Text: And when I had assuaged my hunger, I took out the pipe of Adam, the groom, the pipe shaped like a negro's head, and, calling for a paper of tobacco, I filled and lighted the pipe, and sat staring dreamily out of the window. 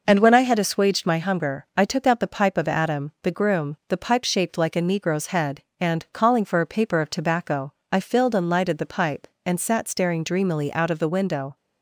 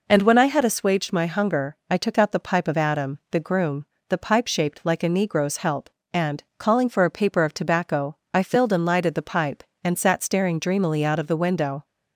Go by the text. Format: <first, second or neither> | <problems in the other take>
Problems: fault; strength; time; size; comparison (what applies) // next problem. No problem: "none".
first | says "help" for "head"; at 5.5 s